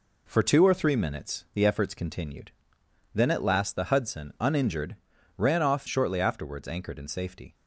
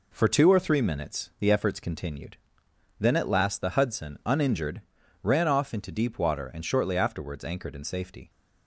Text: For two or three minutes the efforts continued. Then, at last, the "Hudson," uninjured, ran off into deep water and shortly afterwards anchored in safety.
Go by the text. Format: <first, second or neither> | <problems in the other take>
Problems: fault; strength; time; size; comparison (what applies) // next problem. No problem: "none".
second | skips "into deep water and"; at 5.8 s